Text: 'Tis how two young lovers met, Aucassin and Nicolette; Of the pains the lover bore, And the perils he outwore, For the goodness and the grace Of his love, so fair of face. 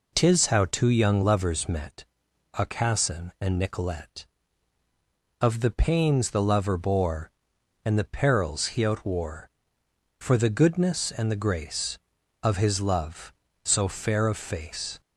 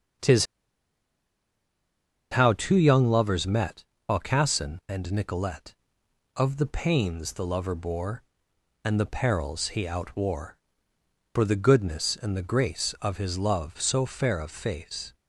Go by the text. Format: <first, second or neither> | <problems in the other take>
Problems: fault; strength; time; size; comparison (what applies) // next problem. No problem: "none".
first | starts louder than the rest; strong; until 3.0 s; 7 dB // pauses between "Tis" and "how"; strong; at 0.4 s; 1.8 s long